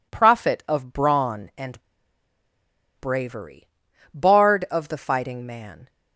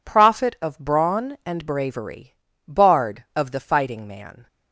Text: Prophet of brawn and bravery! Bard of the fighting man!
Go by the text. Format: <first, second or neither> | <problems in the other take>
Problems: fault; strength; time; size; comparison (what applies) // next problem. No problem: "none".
second | pauses between "and" and "bravery"; at 1.8 s; 1.1 s long